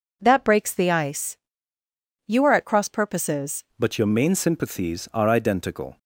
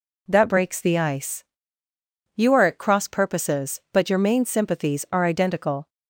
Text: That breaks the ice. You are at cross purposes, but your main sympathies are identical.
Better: second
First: changes voice at "but"; from 3.7 s on; 2.2 s long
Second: none

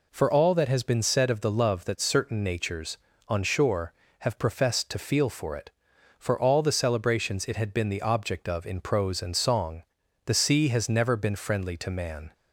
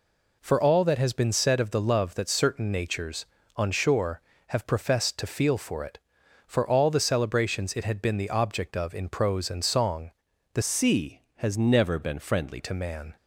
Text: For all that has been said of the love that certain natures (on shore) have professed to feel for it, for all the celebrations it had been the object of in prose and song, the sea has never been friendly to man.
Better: first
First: none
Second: changes voice from "sea" to "friendly"; from 10.6 to 12.5 s; 1.9 s long

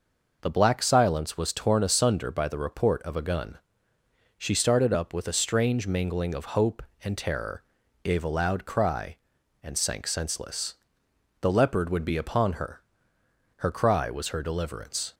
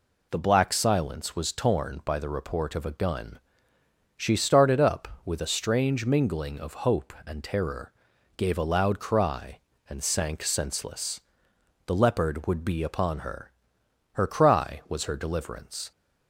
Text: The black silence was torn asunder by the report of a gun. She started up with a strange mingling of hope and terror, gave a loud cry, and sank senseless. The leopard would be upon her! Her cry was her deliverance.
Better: first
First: none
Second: skips "asunder"; at 2.0 s

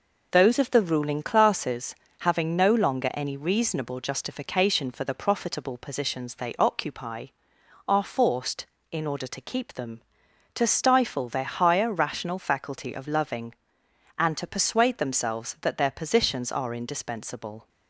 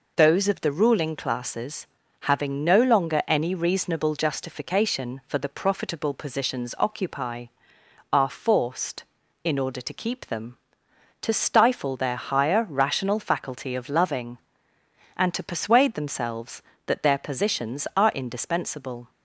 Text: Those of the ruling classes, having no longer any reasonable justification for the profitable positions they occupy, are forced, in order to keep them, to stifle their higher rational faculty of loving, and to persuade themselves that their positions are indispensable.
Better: first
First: none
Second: skips "they"; at 6.7 s

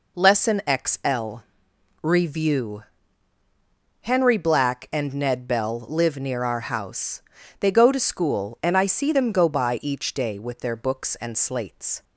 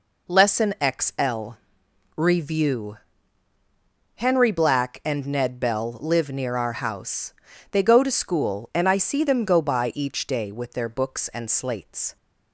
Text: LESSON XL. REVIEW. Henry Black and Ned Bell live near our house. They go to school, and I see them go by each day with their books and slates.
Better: neither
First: none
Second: none

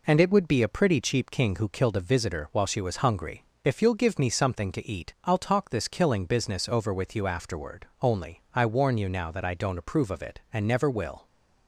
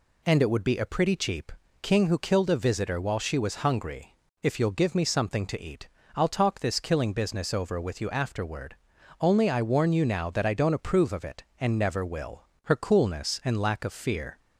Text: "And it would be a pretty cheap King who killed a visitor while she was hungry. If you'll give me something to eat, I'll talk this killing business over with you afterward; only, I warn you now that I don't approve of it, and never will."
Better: first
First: none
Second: pauses between "cheap" and "King"; slight; at 1.5 s; 0.30 s long // goes on to say "Her coolness and lack of fear"; strong; from 12.6 s on; 1.7 s long

